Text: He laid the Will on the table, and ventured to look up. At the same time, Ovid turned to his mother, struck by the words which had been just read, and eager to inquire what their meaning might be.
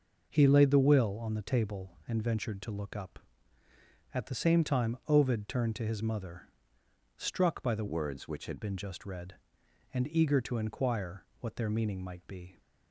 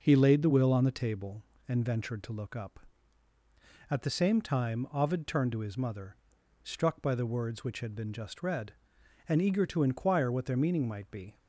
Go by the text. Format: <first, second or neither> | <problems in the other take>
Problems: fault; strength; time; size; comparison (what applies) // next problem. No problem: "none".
second | changes voice from "words" to "had"; from 7.8 to 8.6 s; 0.8 s long // pauses between "inquire" and "what"; slight; at 11.2 s; 0.16 s long